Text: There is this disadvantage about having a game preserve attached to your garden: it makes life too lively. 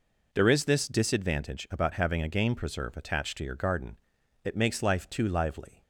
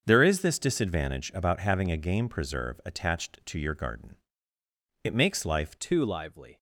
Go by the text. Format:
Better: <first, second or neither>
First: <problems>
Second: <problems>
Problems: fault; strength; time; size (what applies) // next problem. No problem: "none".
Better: first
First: none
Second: starts louder than the rest; until 1.0 s; 7 dB // changes voice at "too"; from 5.7 s on; 0.8 s long